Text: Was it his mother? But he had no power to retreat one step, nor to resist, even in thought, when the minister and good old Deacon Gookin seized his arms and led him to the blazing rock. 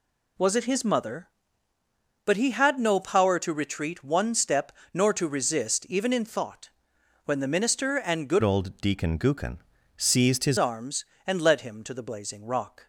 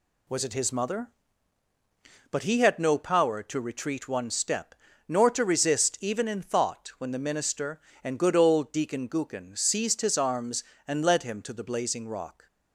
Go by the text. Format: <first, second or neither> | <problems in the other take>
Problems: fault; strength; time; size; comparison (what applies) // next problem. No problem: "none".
second | changes voice from "old" to "his"; from 8.4 to 10.5 s; 2.1 s long // pauses between "Gookin" and "seized"; at 9.5 s; 0.38 s long